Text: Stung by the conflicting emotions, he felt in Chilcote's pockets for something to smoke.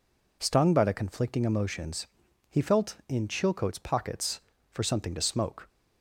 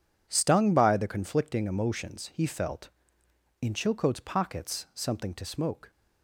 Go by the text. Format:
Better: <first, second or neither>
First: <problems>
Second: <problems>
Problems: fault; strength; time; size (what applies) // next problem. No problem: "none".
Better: first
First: none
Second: skips "for"; at 4.8 s